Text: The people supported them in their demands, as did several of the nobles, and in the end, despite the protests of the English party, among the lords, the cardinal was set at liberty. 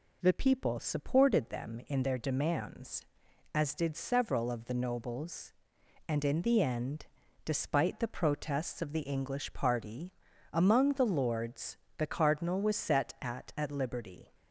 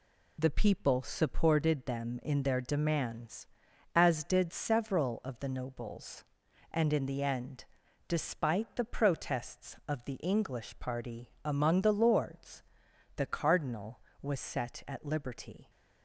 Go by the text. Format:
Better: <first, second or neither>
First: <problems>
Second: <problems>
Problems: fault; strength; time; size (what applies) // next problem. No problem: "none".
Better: second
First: says "at" twice; at 13.5 s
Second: none